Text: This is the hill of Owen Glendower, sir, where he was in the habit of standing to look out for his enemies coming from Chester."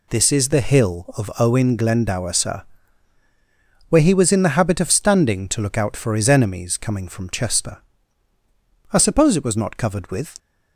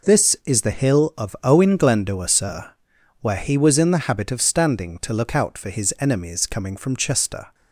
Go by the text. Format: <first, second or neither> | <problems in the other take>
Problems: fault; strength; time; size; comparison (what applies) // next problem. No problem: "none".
second | goes on to say "I suppose it was not covered with"; from 8.9 s on; 1.4 s long